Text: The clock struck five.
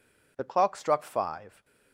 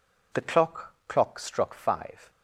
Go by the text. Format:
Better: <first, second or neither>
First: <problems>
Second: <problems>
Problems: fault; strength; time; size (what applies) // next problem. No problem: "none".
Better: first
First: none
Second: says "clock" twice; at 1.0 s